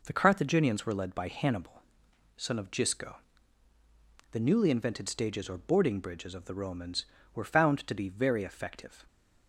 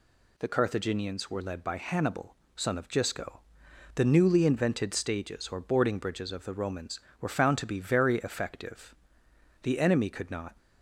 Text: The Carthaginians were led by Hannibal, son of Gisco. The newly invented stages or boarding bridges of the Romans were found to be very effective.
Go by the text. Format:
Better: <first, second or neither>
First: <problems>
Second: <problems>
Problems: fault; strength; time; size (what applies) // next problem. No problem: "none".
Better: first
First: none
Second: goes on to say "The enemy could not"; noticeable; from 9.6 s on; 0.94 s long